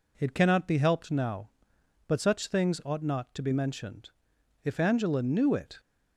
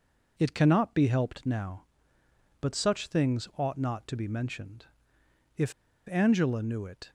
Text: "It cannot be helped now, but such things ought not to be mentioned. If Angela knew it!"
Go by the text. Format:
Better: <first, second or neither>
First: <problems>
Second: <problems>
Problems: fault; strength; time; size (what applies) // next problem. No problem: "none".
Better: first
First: none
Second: pauses between "If" and "Angela"; at 5.7 s; 0.39 s long